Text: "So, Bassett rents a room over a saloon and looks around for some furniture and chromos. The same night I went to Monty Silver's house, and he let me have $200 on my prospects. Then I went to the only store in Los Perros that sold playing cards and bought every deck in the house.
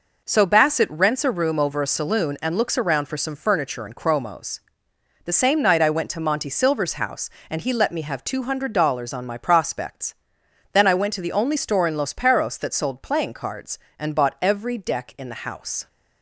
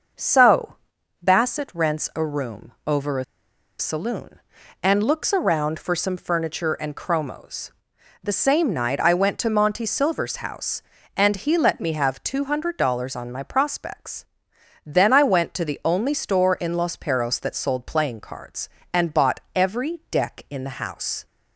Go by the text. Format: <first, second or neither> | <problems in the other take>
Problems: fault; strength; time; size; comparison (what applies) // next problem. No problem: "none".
first | starts louder than the rest; noticeable; until 1.6 s; 6 dB // pauses between "room" and "over"; slight; at 2.7 s; 0.16 s long // pauses between "a" and "saloon"; noticeable; at 3.2 s; 0.54 s long // pauses between "bought" and "every"; slight; at 19.3 s; 0.16 s long